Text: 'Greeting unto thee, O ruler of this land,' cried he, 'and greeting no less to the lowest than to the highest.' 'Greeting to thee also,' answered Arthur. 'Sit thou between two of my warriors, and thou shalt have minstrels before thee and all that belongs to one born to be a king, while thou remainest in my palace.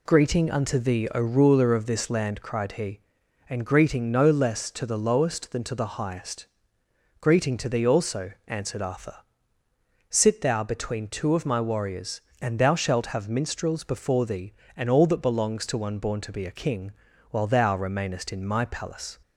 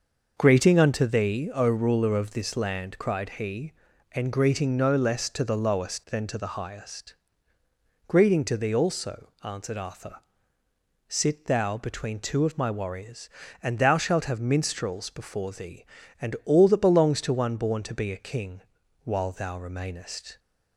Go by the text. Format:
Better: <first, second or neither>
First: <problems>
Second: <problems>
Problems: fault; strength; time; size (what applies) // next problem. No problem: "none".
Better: first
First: none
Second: starts louder than the rest; noticeable; until 1.3 s; 6 dB // stops before "in my palace"; at 20.3 s